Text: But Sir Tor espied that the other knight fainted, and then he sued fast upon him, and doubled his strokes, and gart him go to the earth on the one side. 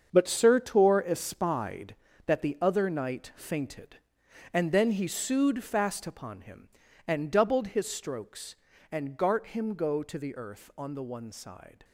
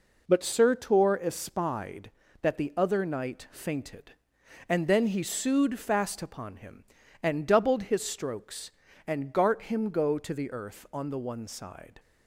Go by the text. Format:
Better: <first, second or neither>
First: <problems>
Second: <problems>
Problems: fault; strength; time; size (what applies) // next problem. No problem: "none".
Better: second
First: gets quieter; strong; throughout; 10.5 dB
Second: none